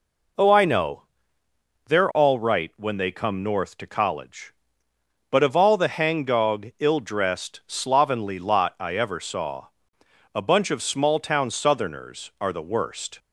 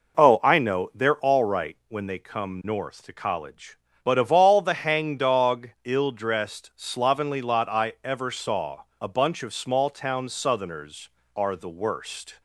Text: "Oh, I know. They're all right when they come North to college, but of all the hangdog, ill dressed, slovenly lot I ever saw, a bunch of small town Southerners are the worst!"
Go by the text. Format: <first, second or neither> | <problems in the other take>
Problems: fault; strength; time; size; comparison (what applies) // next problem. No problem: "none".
neither | none